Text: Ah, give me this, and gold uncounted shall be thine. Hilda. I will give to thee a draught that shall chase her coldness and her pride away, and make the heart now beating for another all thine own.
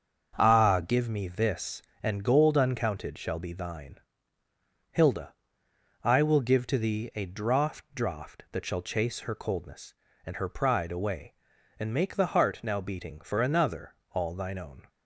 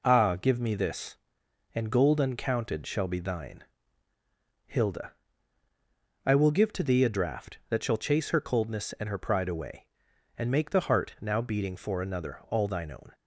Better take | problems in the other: second | starts louder than the rest; until 1.3 s; 6.5 dB // says "draught" twice; at 7.9 s // pauses between "another" and "all"; slight; at 13.9 s; 0.18 s long

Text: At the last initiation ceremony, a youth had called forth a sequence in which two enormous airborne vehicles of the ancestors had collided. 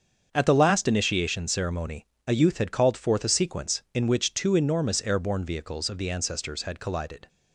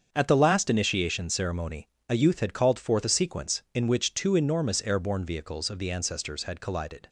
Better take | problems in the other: neither | starts louder than the rest; the same in both

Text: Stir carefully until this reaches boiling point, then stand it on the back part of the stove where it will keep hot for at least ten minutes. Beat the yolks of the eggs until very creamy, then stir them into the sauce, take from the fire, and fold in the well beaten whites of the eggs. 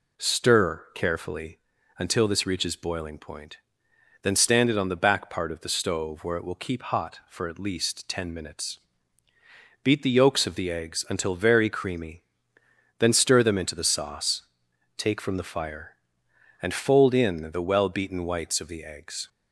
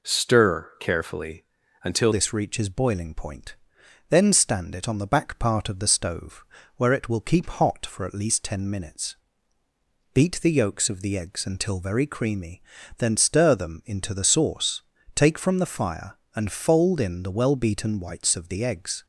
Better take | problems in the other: first | pauses between "carefully" and "until"; at 1.4 s; 0.38 s long; also in the first // changes voice at "this"; from 2.1 s on; 16.9 s long // pauses between "stove" and "where"; slight; at 6.4 s; 0.32 s long

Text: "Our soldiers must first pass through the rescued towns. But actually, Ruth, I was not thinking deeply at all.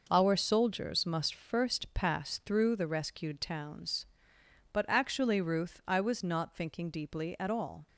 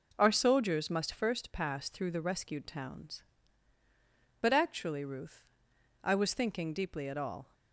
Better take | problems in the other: first | skips "not"; at 6.3 s

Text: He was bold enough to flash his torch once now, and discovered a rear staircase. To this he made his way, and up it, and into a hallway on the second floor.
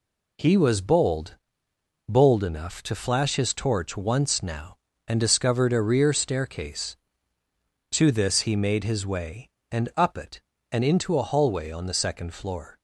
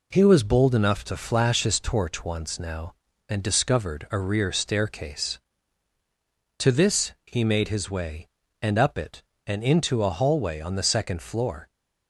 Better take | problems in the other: second | says "bold" twice; at 2.0 s

